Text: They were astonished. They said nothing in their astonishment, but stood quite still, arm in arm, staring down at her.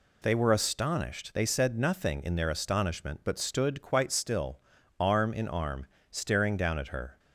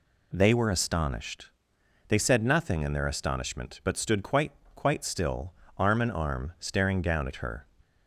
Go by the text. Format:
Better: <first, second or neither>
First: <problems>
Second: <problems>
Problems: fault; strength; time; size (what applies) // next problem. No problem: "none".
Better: first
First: none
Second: says "quite" twice; at 4.7 s